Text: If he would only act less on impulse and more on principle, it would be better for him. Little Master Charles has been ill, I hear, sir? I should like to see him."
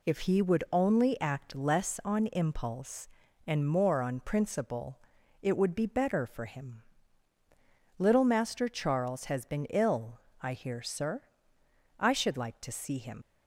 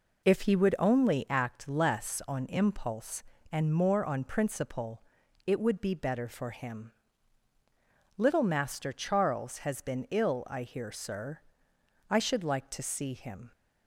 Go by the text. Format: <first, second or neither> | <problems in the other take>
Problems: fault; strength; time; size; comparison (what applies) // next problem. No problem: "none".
second | leaves "him" unfinished; at 13.2 s; 90 ms